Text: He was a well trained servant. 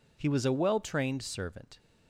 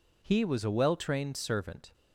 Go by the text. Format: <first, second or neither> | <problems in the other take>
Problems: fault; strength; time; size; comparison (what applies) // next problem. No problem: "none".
neither | none